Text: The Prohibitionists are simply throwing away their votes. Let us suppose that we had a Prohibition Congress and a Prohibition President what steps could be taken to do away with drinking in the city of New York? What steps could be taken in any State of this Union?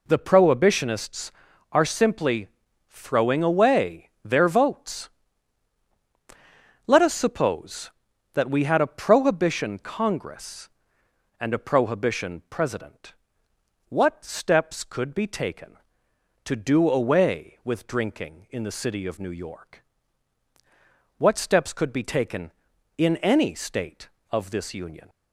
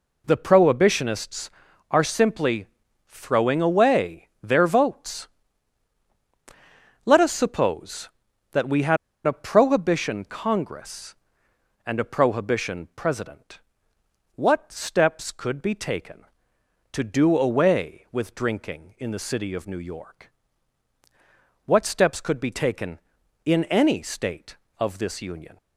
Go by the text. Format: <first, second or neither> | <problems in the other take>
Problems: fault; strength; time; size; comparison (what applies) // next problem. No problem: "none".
first | pauses between "simply" and "throwing"; at 2.6 s; 0.42 s long; also in the first // pauses between "had" and "a"; slight; at 8.9 s; 0.29 s long // pauses between "President" and "what"; noticeable; at 13.5 s; 0.76 s long; noticeable in the first